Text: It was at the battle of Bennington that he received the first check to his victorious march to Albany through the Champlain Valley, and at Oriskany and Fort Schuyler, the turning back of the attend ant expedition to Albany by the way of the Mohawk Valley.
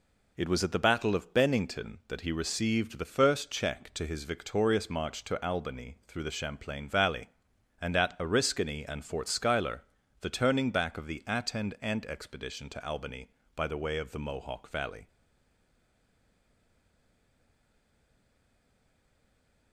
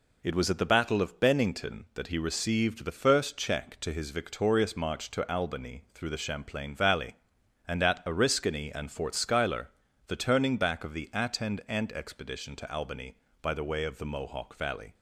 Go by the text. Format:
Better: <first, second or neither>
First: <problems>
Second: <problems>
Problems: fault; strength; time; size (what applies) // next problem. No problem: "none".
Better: second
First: stays silent after the last word; strong; from 15.0 s on; 4.7 s long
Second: none